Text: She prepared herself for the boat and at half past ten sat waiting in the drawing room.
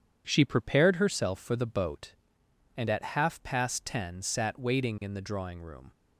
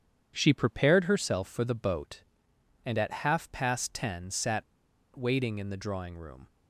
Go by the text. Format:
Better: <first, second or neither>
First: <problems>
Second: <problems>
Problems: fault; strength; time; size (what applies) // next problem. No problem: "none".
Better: first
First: none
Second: pauses between "sat" and "waiting"; noticeable; at 4.6 s; 0.53 s long